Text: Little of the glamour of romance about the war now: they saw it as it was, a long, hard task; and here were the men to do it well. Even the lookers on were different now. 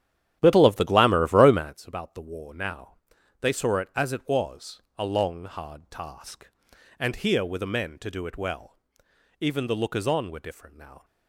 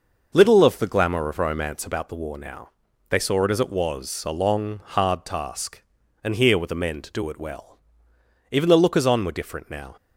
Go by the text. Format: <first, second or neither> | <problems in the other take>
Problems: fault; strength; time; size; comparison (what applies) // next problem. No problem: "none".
second | starts louder than the rest; strong; until 1.8 s; 11 dB